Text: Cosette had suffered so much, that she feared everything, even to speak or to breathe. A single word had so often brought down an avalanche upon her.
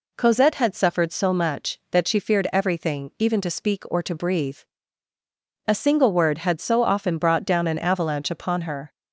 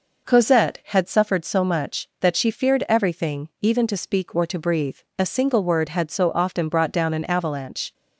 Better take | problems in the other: first | stops before "upon her"; at 7.9 s

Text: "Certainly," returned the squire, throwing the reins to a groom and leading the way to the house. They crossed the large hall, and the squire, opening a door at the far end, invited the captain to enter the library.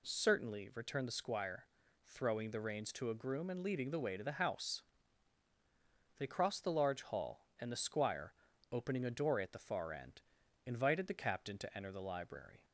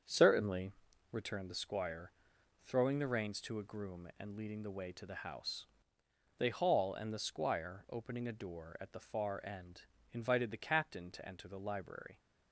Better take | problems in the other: first | starts louder than the rest; strong; until 1.4 s; 7.5 dB // skips "crossed the large"; at 6.4 s

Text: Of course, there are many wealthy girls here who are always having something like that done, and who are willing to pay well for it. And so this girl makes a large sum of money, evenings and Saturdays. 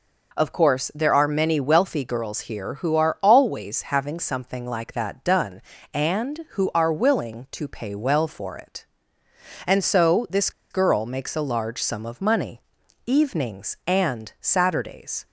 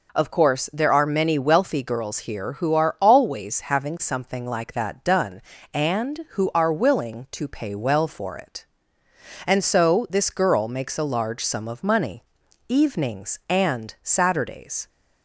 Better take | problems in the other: second | pauses between "this" and "girl"; slight; at 10.5 s; 0.20 s long

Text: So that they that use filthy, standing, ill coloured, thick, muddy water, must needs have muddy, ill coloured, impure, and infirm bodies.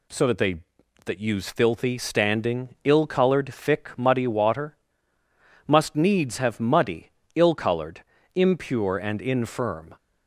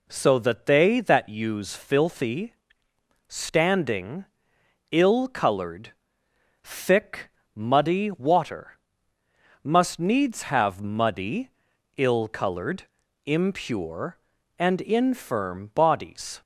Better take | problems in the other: second | stops before "bodies"; at 9.9 s

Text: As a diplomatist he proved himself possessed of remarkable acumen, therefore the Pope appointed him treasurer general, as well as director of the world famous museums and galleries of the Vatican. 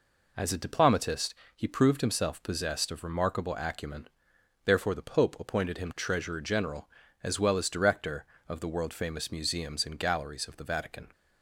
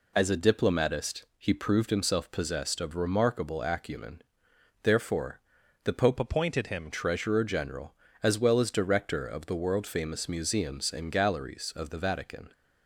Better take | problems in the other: first | pauses between "diplomatist" and "he"; slight; at 1.2 s; 0.16 s long; slight in the first // pauses between "therefore" and "the"; noticeable; at 5.3 s; 0.46 s long // changes voice from "appointed" to "him"; from 6.1 to 6.9 s; 0.8 s long

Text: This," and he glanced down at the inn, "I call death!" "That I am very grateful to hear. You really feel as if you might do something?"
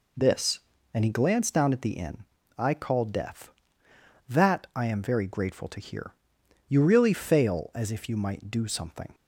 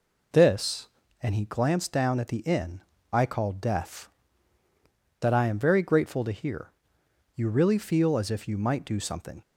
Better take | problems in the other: second | says "fail" for "feel"; at 7.1 s

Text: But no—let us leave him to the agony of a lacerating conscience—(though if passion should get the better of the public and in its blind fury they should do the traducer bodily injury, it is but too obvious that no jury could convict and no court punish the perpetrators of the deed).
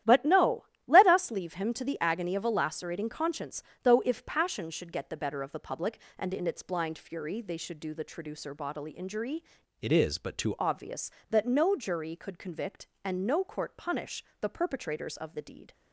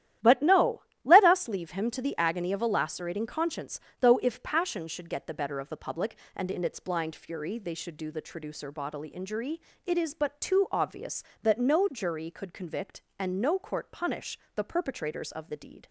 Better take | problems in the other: second | starts louder than the rest; strong; until 1.3 s; 12 dB; strong in the second // changes voice from "it" to "too"; from 9.8 to 10.5 s; 0.7 s long // pauses between "punish" and "the"; slight; at 14.2 s; 0.20 s long; slight in the second

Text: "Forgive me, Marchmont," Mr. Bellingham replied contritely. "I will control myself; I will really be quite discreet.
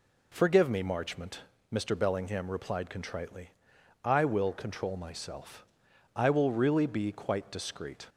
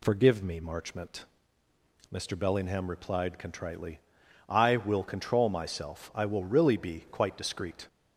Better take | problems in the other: neither | none

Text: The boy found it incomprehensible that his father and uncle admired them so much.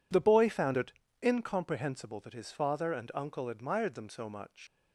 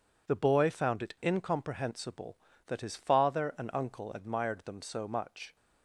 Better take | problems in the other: second | pauses between "it" and "incomprehensible"; slight; at 0.9 s; 0.32 s long // leaves "much" unfinished; at 4.6 s; 75 ms

